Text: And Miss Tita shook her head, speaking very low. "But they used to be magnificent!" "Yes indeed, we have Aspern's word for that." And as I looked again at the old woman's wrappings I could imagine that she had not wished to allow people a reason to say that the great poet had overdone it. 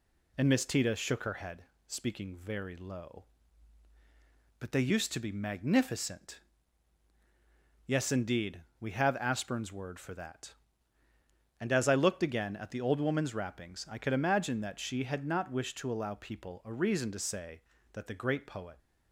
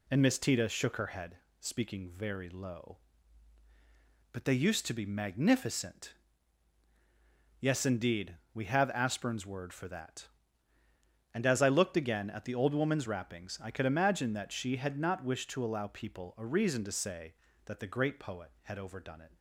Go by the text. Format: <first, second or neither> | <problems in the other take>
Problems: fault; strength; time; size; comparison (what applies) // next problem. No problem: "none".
second | stops before "had overdone it"; at 18.7 s